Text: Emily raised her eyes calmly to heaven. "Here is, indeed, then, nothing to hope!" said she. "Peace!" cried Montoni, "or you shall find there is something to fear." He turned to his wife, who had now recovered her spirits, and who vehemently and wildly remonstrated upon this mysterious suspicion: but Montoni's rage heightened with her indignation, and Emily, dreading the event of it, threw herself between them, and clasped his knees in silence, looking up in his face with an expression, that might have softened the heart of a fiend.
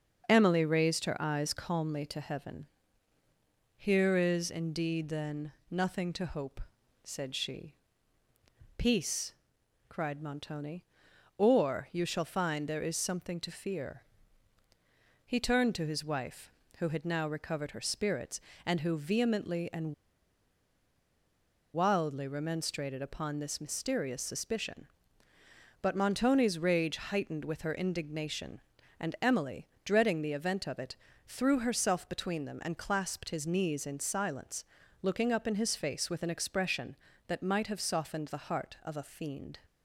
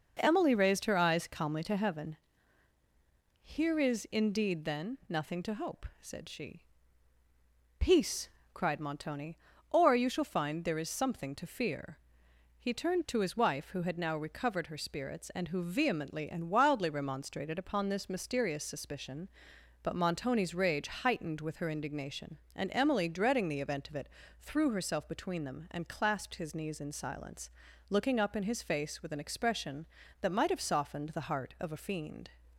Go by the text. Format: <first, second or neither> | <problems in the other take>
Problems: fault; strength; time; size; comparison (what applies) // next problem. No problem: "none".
second | starts louder than the rest; until 1.2 s; 6.5 dB // pauses between "and" and "wildly"; strong; at 19.9 s; 1.8 s long